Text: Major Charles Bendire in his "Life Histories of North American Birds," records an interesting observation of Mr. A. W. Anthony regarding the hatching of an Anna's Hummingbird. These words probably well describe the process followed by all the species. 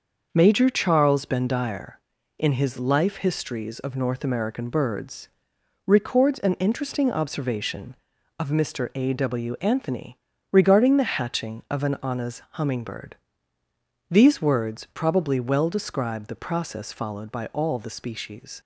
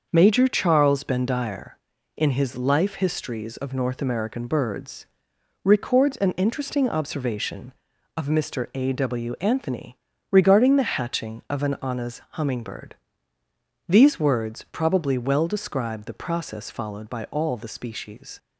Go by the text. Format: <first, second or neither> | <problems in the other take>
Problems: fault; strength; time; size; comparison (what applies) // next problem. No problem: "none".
neither | starts louder than the rest; the same in both // pauses between "Anthony" and "regarding"; slight; the same in both